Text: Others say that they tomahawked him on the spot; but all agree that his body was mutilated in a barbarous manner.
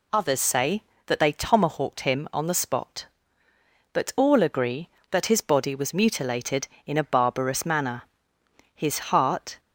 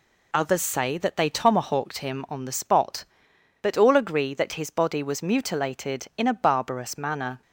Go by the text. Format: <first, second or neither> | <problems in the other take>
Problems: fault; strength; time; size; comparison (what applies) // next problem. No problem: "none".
second | goes on to say "His heart"; noticeable; from 8.7 s on; 0.86 s long